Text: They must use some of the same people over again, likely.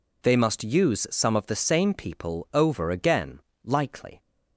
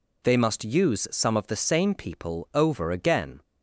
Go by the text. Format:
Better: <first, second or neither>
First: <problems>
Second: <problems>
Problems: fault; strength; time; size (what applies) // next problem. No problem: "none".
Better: first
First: none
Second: stops before "likely"; at 3.4 s